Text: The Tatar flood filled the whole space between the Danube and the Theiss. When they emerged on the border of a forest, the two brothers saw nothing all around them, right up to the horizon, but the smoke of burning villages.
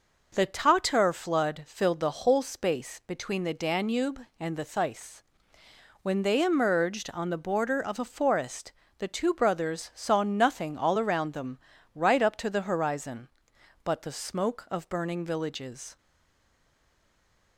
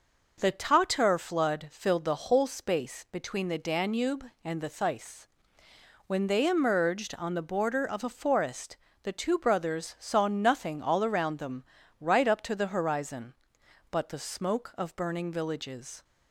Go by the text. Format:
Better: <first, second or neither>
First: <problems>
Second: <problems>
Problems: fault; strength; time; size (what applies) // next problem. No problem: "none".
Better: second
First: stays silent after the last word; noticeable; from 15.9 s on; 1.6 s long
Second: none